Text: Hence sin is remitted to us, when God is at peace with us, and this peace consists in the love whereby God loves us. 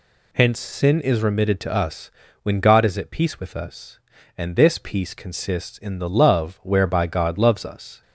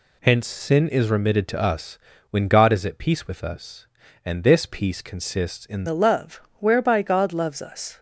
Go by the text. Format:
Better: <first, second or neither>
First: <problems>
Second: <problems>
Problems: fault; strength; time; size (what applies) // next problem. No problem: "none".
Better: first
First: none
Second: changes voice at "the"; from 5.8 s on; 2.1 s long // pauses between "love" and "whereby"; slight; at 6.3 s; 0.22 s long